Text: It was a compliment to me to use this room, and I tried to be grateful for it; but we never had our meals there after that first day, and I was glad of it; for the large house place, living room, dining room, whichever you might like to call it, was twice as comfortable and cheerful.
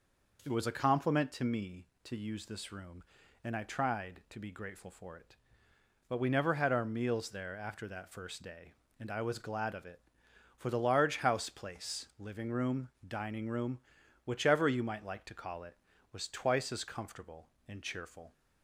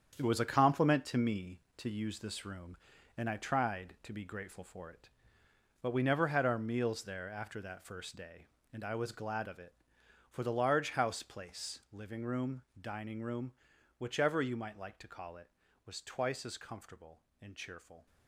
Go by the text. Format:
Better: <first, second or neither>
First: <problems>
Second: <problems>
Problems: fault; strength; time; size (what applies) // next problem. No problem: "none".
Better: first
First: none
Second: gets quieter; strong; throughout; 9.5 dB